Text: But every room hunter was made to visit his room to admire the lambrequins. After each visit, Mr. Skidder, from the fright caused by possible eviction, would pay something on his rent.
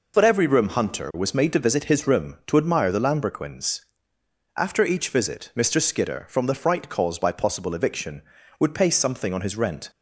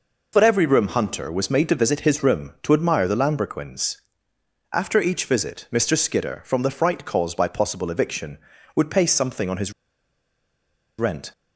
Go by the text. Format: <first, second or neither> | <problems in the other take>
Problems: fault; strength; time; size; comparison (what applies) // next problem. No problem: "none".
first | pauses between "his" and "rent"; strong; at 9.7 s; 1.2 s long